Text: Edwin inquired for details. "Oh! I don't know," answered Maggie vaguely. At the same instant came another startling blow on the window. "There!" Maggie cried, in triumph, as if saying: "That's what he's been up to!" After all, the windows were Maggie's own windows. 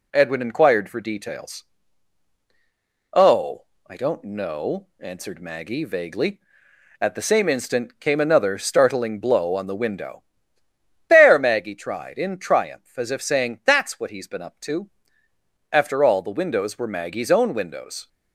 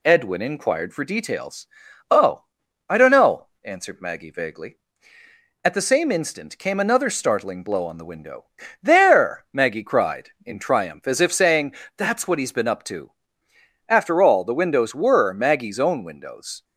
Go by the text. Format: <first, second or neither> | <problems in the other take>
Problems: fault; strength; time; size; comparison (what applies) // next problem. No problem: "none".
second | says "tried" for "cried"; at 11.7 s